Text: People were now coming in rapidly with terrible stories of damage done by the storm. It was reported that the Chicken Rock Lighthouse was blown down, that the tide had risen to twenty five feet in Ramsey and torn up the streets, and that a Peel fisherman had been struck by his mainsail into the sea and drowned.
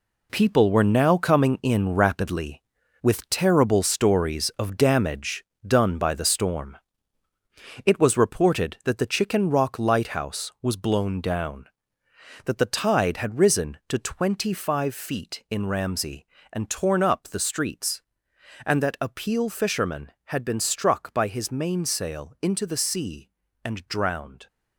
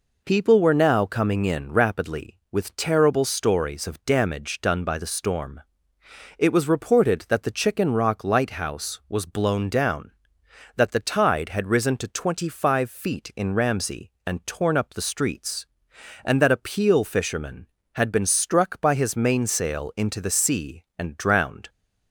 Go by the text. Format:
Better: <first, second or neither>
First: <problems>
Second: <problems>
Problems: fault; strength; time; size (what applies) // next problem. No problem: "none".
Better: second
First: gets quieter; strong; throughout; 8 dB // pauses between "damage" and "done"; slight; at 5.4 s; 0.24 s long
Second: none